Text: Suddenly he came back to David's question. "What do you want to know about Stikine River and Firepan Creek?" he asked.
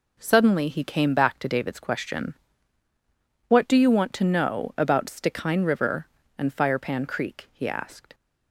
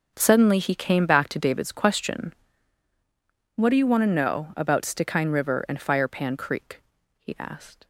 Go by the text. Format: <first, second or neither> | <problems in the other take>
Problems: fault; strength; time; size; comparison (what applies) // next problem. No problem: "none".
first | gets quieter; strong; throughout; 15.5 dB